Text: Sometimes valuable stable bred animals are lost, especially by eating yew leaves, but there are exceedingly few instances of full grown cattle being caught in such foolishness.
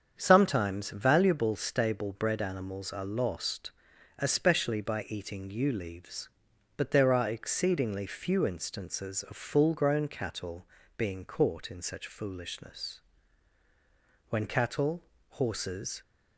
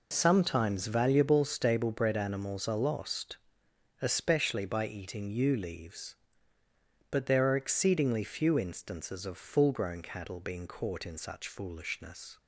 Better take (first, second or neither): second